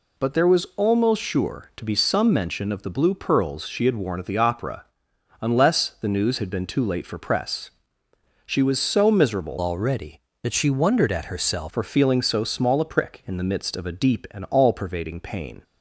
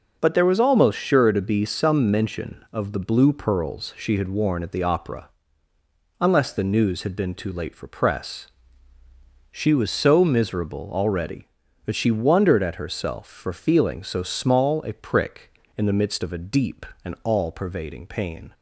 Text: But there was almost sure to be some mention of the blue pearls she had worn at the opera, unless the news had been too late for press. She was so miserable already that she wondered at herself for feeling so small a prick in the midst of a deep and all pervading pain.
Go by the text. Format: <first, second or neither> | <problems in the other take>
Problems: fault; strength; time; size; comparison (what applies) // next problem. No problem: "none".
second | changes voice from "already" to "herself"; from 9.5 to 11.7 s; 2.2 s long